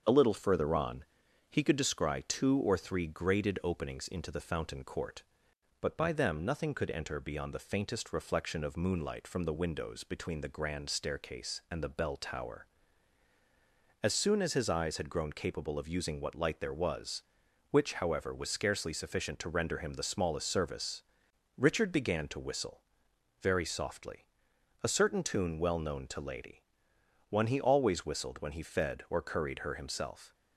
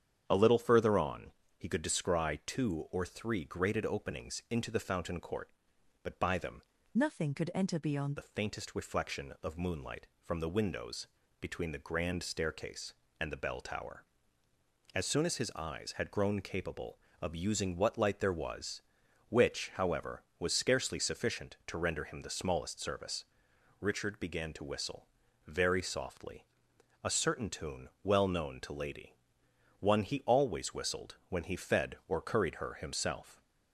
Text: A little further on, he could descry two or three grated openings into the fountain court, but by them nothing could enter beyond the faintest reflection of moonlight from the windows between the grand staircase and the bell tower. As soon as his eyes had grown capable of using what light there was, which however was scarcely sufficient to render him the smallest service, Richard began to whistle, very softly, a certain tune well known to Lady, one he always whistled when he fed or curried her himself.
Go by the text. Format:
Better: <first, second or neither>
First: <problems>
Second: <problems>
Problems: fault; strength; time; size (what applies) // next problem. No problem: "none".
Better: first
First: starts louder than the rest; until 1.0 s; 7 dB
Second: starts louder than the rest; strong; until 1.2 s; 9 dB // changes voice from "nothing" to "beyond"; from 6.9 to 8.1 s; 1.2 s long // pauses between "windows" and "between"; slight; at 11.0 s; 0.34 s long